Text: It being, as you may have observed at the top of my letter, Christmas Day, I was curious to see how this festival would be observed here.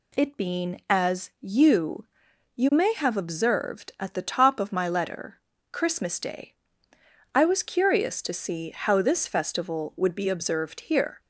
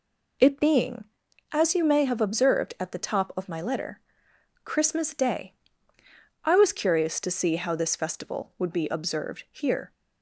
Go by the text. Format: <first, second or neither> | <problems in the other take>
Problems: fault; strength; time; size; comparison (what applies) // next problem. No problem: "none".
second | says "you" twice; at 2.5 s